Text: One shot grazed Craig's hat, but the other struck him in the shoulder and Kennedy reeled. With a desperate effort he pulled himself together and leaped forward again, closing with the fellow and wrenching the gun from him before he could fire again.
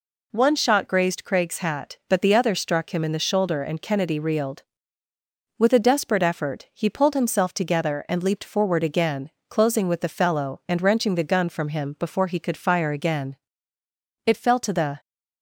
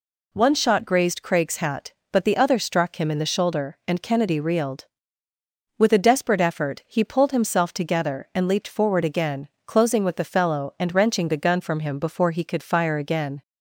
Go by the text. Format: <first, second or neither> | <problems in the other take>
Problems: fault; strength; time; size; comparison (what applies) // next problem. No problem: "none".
second | goes on to say "It fell to the"; noticeable; from 14.2 s on; 0.74 s long